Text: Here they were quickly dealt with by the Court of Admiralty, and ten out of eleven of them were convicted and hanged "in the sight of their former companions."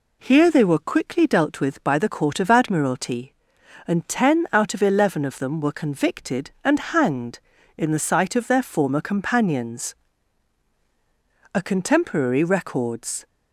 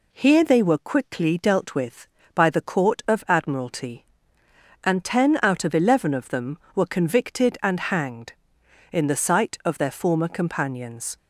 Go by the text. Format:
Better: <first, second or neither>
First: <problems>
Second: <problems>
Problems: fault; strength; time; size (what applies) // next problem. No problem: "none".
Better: second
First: goes on to say "A contemporary records"; strong; from 11.5 s on; 1.7 s long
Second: none